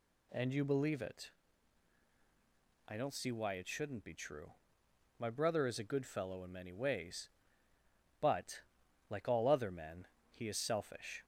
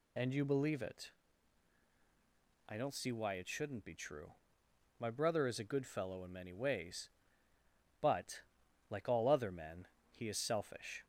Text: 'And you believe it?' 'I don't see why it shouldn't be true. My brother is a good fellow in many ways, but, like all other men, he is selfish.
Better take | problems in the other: first | loses the start of "And"; at 0.1 s; 45 ms

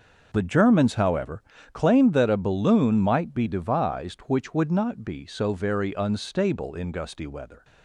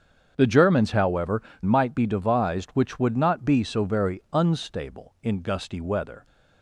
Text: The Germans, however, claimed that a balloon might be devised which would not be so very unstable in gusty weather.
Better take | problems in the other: first | starts louder than the rest; strong; until 1.3 s; 7.5 dB // skips "claimed that a balloon"; at 1.5 s

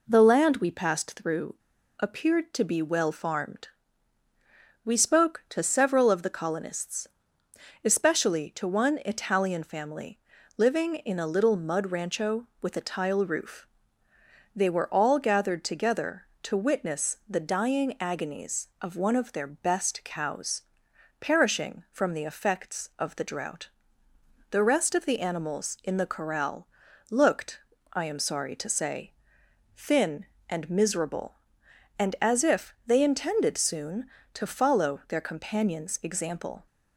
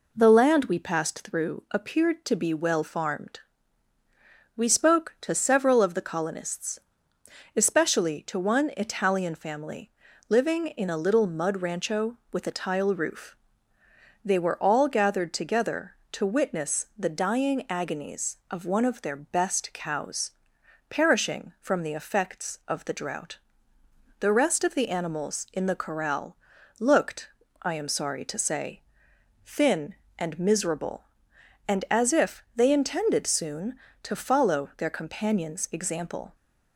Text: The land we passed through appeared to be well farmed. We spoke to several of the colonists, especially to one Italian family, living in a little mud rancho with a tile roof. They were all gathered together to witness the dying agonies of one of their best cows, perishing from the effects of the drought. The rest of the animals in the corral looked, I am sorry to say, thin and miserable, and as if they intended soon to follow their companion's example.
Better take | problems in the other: second | pauses between "through" and "appeared"; at 1.5 s; 0.44 s long // pauses between "corral" and "looked"; noticeable; at 26.6 s; 0.46 s long; noticeable in the second

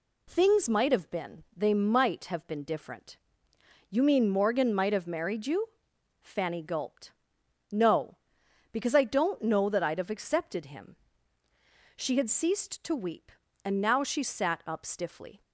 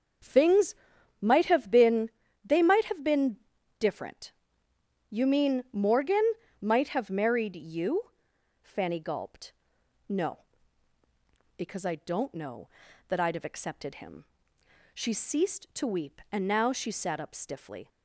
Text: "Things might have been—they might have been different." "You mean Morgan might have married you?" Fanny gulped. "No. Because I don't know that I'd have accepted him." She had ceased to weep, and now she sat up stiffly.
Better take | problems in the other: first | starts louder than the rest; until 1.7 s; 6.5 dB // pauses between "Things" and "might"; noticeable; at 0.7 s; 0.48 s long // pauses between "been" and "different"; at 3.3 s; 0.42 s long // pauses between "Morgan" and "might"; at 6.2 s; 0.38 s long // skips "had"; at 15.1 s

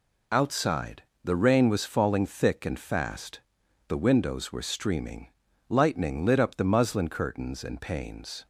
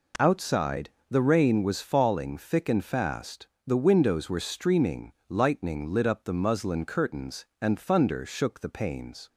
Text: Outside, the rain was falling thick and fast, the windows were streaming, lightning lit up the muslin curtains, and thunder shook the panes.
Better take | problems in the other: second | skips "thunder shook the"; at 7.7 s

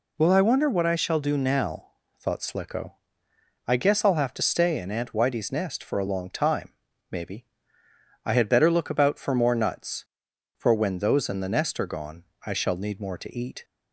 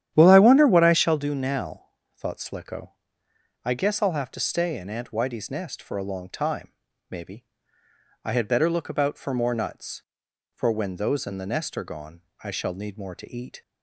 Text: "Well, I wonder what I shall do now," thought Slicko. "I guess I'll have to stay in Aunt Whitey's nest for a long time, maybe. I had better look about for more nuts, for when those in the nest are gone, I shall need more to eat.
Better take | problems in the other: first | starts louder than the rest; strong; until 1.3 s; 10.5 dB

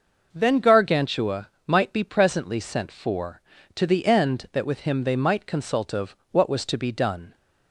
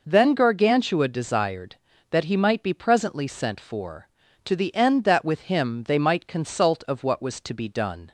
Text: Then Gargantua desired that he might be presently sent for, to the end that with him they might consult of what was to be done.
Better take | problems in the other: second | skips "desired that he"; at 1.5 s // pauses between "of" and "what"; slight; at 6.1 s; 0.16 s long

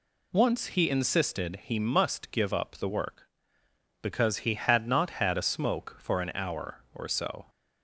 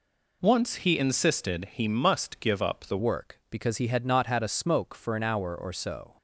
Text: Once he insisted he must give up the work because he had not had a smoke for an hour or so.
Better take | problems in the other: first | changes voice at "work"; from 2.9 s on; 3.2 s long

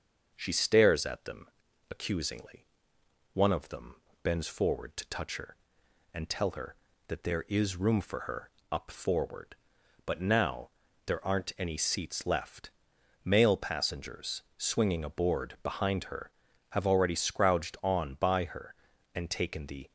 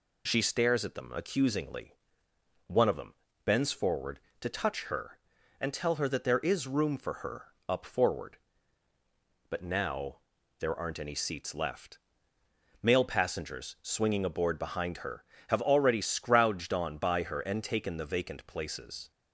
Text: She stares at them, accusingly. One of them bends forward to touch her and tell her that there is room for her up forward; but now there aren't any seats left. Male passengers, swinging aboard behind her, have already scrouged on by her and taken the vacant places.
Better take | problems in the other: second | starts louder than the rest; until 1.3 s; 6.5 dB // pauses between "them" and "bends"; slight; at 3.9 s; 0.28 s long; slight in the second // pauses between "her" and "up"; slight; at 8.5 s; 0.20 s long // pauses between "now" and "there"; slight; at 10.7 s; 0.34 s long; also in the second // stops before "vacant places"; at 19.8 s

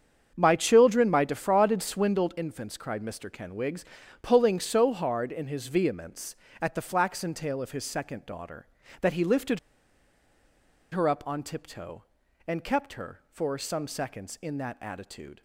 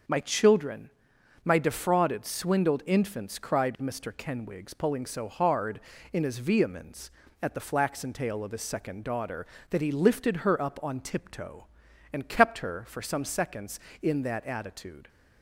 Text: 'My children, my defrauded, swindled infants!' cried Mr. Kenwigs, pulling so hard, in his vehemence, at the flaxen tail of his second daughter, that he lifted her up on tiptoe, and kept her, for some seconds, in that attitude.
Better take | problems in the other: second | starts louder than the rest; strong; until 1.3 s; 7.5 dB; also in the second // pauses between "lifted" and "her"; strong; at 9.5 s; 1.3 s long

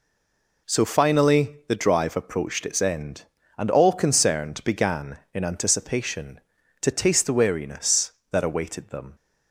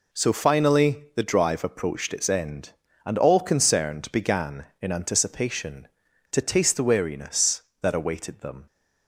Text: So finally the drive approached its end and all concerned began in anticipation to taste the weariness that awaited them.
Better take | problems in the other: second | stays silent before the first word; slight; until 0.6 s; 0.6 s long

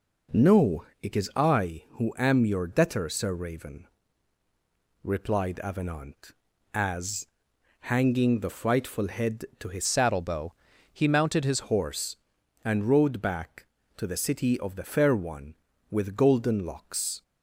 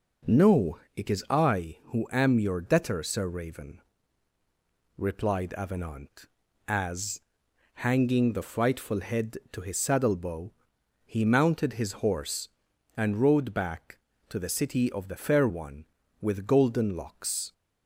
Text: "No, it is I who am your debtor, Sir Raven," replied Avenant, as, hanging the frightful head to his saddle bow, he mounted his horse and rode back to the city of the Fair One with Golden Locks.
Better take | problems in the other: second | changes voice from "saddle" to "his"; from 9.8 to 11.5 s; 1.7 s long

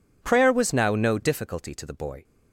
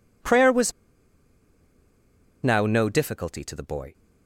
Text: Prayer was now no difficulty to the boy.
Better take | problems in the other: first | pauses between "was" and "now"; strong; at 0.7 s; 1.7 s long

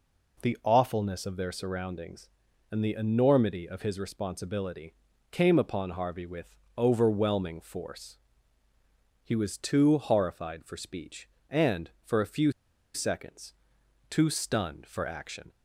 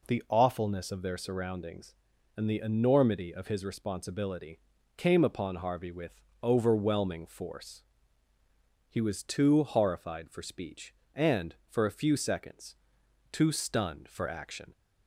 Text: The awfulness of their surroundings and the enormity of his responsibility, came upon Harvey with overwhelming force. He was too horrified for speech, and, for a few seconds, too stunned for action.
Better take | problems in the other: second | pauses between "with" and "overwhelming"; slight; at 6.5 s; 0.22 s long; slight in the second // pauses between "few" and "seconds"; at 12.5 s; 0.42 s long

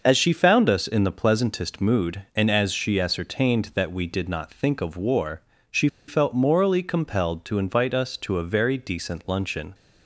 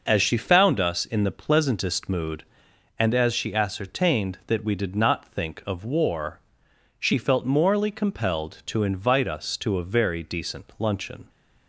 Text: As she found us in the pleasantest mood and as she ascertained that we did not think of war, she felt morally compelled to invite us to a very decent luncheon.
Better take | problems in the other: second | pauses between "she" and "felt"; slight; at 5.8 s; 0.21 s long

